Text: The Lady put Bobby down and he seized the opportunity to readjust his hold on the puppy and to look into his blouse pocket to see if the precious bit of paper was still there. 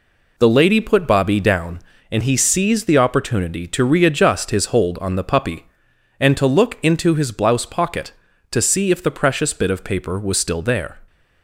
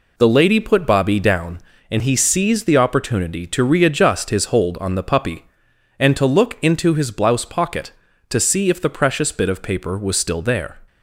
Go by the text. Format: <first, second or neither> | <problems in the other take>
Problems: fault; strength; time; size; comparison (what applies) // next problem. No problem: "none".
neither | none